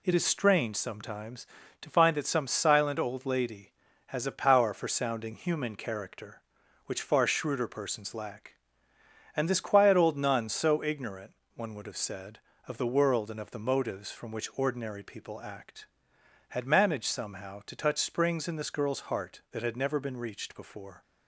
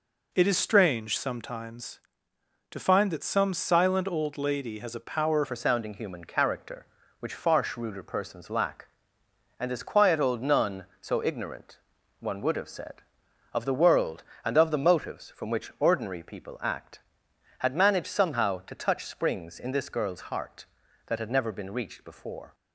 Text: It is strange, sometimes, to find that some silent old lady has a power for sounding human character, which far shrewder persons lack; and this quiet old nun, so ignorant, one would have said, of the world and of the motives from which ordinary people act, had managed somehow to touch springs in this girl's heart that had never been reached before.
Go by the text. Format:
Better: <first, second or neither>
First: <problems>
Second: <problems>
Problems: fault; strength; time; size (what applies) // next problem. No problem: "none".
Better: first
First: none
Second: changes voice at "for"; from 5.4 s on; 17.1 s long